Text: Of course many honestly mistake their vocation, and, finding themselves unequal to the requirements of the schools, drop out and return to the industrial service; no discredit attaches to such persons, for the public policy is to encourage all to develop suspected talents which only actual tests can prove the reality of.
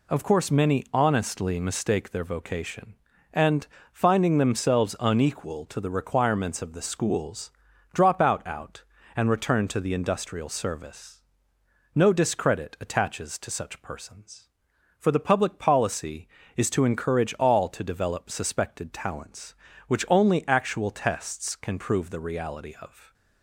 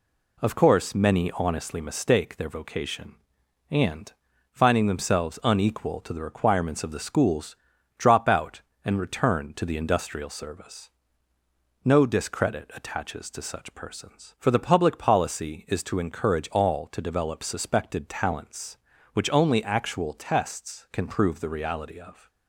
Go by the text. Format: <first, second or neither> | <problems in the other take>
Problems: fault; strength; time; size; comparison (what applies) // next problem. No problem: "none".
second | says "out" twice; at 8.4 s